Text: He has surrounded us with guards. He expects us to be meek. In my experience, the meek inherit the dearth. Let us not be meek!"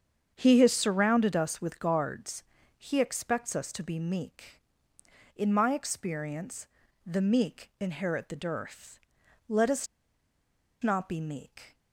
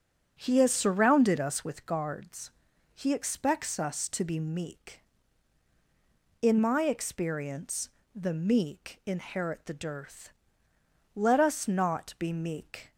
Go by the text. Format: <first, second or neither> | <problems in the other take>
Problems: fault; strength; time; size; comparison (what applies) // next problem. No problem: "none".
second | starts louder than the rest; strong; until 1.3 s; 7.5 dB; strong in the second // pauses between "us" and "not"; noticeable; at 9.8 s; 0.96 s long